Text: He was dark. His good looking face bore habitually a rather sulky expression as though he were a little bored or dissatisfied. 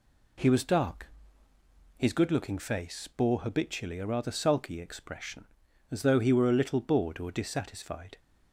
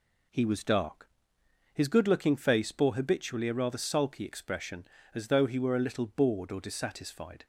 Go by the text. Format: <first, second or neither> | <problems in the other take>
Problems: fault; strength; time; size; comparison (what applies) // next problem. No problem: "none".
neither | none